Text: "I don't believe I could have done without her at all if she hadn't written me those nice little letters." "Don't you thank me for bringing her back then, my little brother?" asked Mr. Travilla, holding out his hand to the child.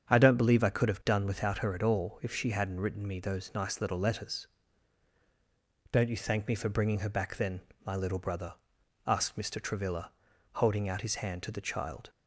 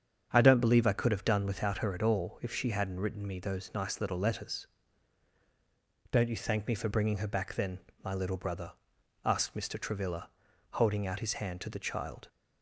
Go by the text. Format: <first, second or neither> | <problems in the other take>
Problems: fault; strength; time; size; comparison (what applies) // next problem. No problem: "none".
neither | starts louder than the rest; strong; the same in both